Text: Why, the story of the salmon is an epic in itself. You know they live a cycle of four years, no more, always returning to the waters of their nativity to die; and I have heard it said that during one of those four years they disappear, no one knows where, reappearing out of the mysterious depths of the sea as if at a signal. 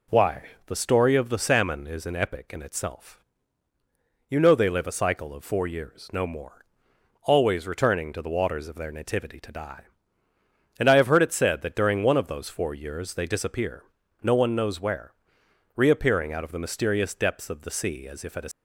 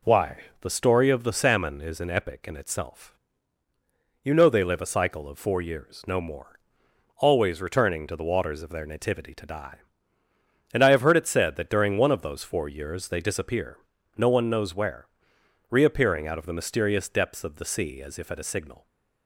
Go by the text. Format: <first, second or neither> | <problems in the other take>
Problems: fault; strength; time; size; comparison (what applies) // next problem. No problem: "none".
second | stops before "signal"; at 18.5 s